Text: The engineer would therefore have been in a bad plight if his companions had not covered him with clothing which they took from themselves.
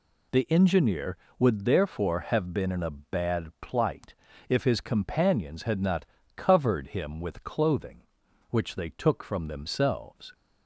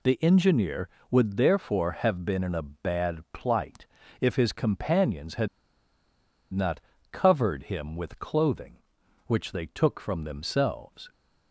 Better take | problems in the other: first | pauses between "plight" and "if"; slight; at 3.8 s; 0.36 s long; slight in the first // pauses between "had" and "not"; at 5.4 s; 1.0 s long // pauses between "not" and "covered"; slight; at 6.7 s; 0.30 s long; slight in the first

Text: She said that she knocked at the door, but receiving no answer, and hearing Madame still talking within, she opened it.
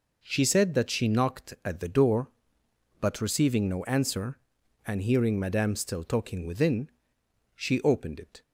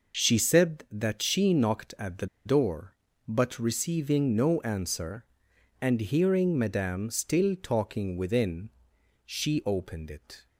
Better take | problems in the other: first | pauses between "the" and "door"; slight; at 2.2 s; 0.19 s long

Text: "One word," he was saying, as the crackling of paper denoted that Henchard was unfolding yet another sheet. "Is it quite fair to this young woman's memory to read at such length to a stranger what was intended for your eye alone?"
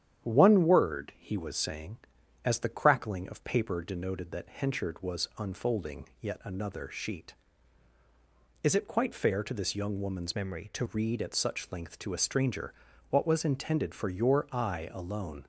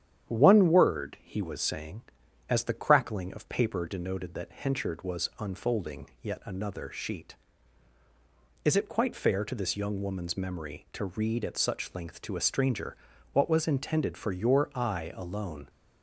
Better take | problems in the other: second | starts louder than the rest; strong; until 1.2 s; 9.5 dB; strong in the second // changes voice from "memory" to "to"; from 10.3 to 10.8 s; 0.5 s long // pauses between "stranger" and "what"; at 12.7 s; 0.38 s long; also in the second

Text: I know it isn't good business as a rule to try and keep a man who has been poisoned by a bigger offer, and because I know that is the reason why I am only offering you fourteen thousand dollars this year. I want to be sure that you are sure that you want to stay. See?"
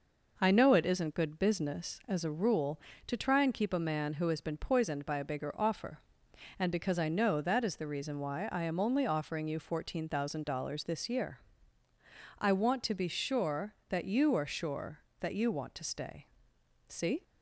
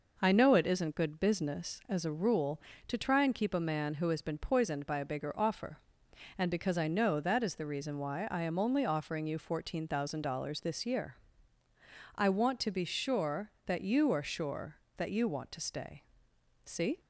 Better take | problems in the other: neither | none

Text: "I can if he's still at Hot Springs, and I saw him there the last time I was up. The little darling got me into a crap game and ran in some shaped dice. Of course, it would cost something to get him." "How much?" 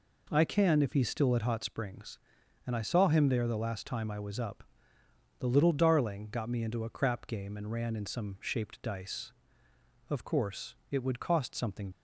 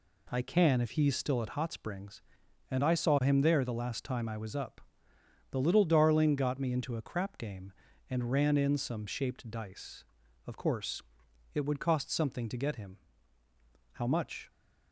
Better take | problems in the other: second | stops before "to get him How much"; at 11.9 s

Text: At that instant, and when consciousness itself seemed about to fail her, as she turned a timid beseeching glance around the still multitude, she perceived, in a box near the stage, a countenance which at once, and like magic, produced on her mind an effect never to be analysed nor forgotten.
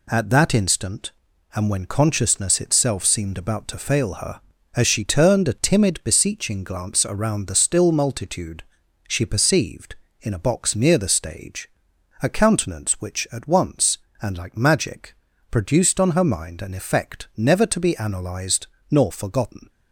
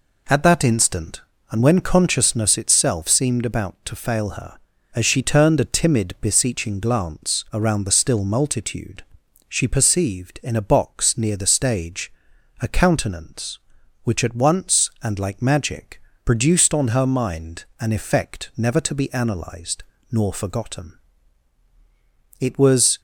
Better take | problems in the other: first | pauses between "analysed" and "nor"; slight; at 19.8 s; 0.28 s long; slight in the first // goes on to say "It was"; noticeable; from 22.3 s on; 0.62 s long

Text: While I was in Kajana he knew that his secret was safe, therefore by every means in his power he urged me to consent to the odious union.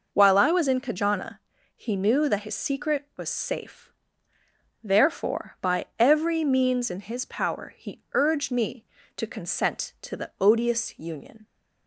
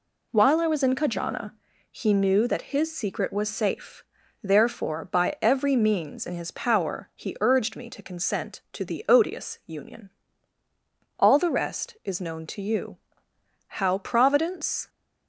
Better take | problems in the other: first | pauses between "Kajana" and "he"; at 1.5 s; 0.38 s long; also in the first // goes on to say "All the rest is known to you how Providence"; strong; from 11.1 s on; 3.7 s long

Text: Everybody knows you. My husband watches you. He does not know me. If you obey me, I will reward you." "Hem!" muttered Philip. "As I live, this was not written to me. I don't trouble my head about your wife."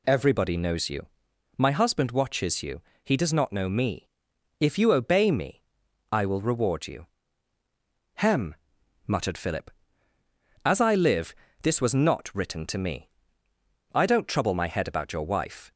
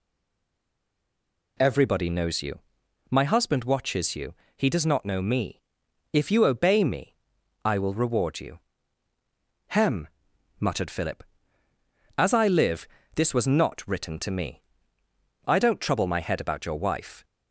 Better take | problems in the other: first | stays silent before the first word; noticeable; until 1.5 s; 1.5 s long

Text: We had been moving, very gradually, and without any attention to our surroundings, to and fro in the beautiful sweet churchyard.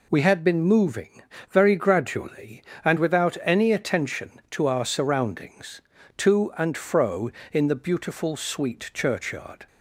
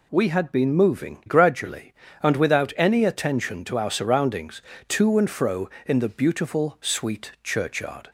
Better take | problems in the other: first | skips "very"; at 1.2 s

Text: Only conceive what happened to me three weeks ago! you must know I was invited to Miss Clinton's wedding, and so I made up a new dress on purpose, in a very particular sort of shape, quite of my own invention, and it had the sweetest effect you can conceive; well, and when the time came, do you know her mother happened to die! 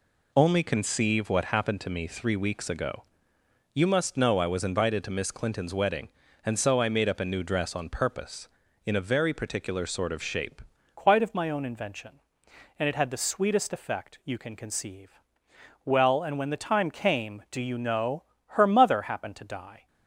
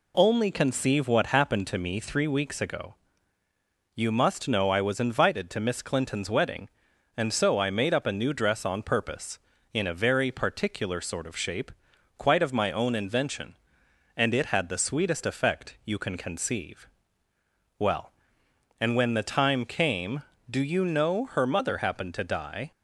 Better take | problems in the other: second | changes voice at "quite"; from 10.9 s on; 8.9 s long // pauses between "know" and "her"; slight; at 18.2 s; 0.26 s long

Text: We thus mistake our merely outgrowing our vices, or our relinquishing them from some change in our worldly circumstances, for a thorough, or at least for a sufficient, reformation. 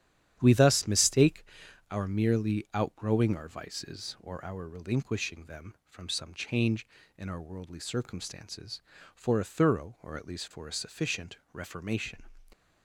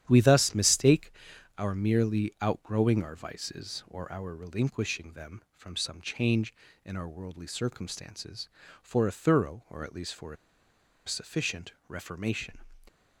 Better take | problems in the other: first | starts louder than the rest; strong; until 1.0 s; 10.5 dB; strong in the first // pauses between "mistake" and "our"; noticeable; at 1.1 s; 0.46 s long; noticeable in the first // pauses between "a" and "sufficient"; noticeable; at 10.3 s; 0.70 s long

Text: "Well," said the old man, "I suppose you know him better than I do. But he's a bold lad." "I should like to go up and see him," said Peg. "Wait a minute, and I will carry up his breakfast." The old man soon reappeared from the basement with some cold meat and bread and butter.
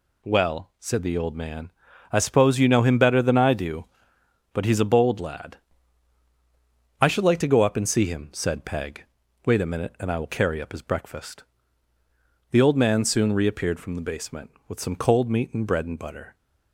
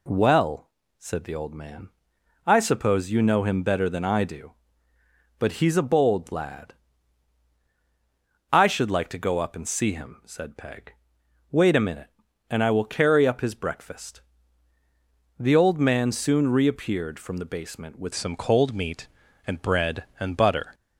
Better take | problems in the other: first | changes voice at "some"; from 18.1 s on; 2.6 s long

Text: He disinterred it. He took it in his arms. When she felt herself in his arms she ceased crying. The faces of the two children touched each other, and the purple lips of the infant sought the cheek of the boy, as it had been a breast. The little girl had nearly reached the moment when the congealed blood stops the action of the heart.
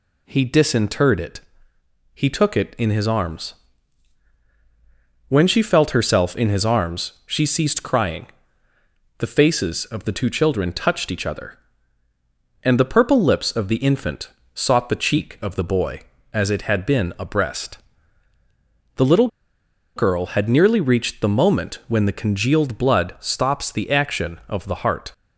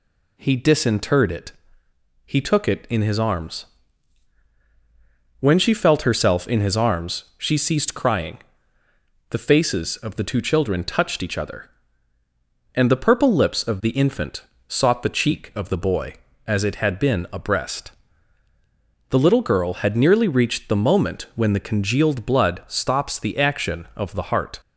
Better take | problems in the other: second | pauses between "infant" and "sought"; slight; at 14.2 s; 0.24 s long; slight in the second // pauses between "little" and "girl"; noticeable; at 19.2 s; 0.67 s long

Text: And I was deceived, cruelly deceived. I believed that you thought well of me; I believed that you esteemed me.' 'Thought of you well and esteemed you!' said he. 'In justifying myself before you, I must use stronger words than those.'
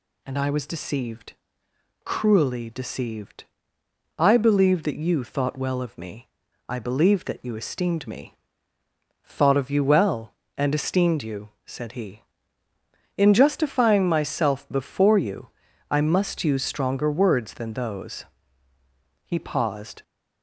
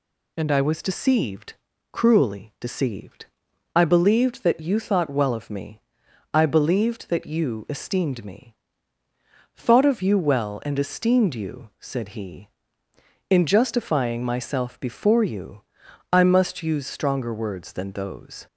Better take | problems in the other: second | goes on to say "He paused"; noticeable; from 19.2 s on; 0.78 s long

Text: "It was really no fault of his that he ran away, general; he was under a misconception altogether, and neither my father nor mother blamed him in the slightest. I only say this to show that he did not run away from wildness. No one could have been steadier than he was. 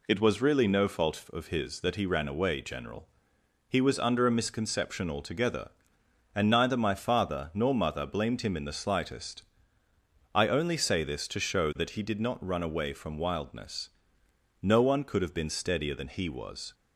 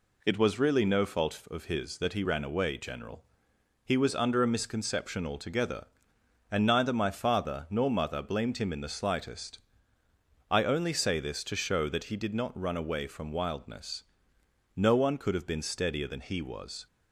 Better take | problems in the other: neither | none

